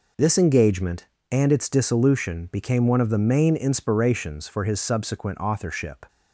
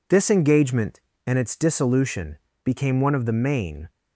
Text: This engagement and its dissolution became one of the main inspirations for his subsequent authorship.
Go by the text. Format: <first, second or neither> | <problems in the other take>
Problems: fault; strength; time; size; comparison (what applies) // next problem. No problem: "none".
first | pauses between "dissolution" and "became"; slight; at 2.3 s; 0.26 s long // stops before "inspirations for his subsequent authorship"; at 3.8 s